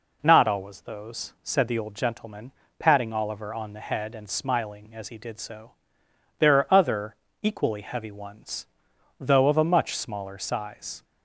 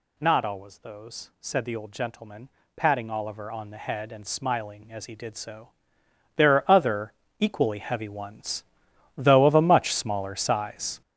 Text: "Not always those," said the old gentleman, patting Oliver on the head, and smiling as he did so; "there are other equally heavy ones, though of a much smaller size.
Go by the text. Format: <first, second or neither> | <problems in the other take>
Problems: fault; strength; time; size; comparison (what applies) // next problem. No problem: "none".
first | gets louder; strong; throughout; 9.5 dB // pauses between "other" and "equally"; slight; at 7.1 s; 0.26 s long; slight in the first